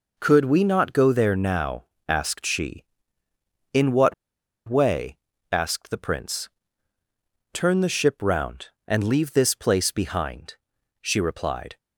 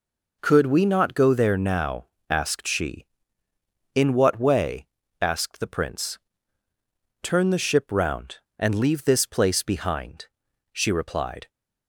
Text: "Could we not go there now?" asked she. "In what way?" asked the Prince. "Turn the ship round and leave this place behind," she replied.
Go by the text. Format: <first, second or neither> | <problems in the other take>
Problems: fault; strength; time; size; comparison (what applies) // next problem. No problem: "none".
second | pauses between "what" and "way"; noticeable; at 4.1 s; 0.54 s long